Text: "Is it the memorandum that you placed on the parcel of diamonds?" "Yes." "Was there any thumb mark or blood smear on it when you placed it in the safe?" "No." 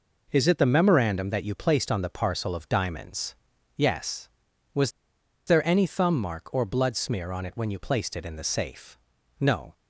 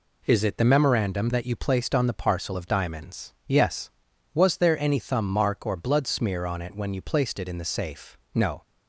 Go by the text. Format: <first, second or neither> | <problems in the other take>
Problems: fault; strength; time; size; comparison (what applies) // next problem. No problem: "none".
second | pauses between "Was" and "there"; noticeable; at 4.9 s; 0.56 s long